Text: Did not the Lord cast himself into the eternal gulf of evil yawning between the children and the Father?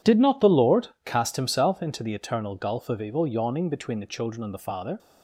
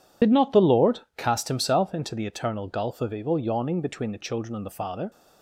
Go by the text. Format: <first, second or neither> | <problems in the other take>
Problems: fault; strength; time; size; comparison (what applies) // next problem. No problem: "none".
first | loses the start of "Did"; at 0.2 s; 55 ms // pauses between "Lord" and "cast"; slight; at 1.0 s; 0.16 s long; slight in the first